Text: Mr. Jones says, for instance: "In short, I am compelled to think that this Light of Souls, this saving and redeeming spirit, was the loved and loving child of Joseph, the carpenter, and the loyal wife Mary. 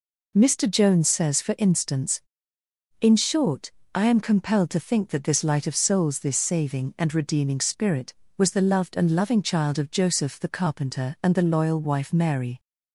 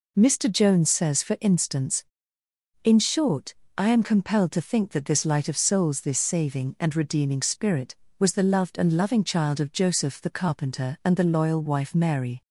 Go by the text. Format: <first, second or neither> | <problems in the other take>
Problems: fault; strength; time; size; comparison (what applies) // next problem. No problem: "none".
neither | none